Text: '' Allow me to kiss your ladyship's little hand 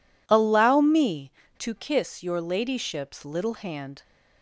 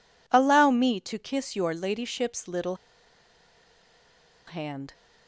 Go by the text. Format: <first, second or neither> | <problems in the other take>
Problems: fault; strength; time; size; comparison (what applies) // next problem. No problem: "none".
first | pauses between "little" and "hand"; strong; at 2.7 s; 1.7 s long